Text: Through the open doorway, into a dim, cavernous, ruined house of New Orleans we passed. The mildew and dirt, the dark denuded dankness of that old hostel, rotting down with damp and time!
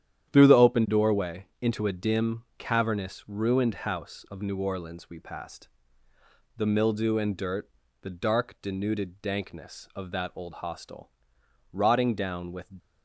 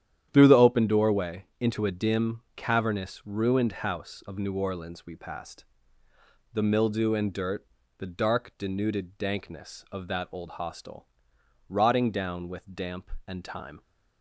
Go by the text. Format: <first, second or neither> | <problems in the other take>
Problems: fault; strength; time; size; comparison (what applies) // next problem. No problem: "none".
second | starts louder than the rest; strong; until 1.3 s; 10.5 dB; strong in the second // stops before "damp and time"; at 12.7 s